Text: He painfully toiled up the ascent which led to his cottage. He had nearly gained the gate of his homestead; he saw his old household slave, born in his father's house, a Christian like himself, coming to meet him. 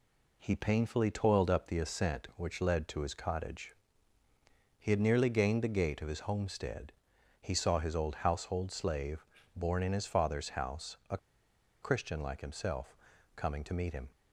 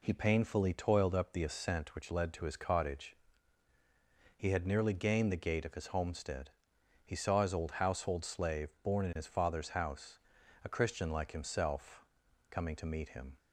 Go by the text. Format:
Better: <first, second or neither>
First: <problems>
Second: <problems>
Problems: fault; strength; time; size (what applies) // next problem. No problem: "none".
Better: second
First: pauses between "a" and "Christian"; noticeable; at 11.1 s; 0.64 s long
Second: none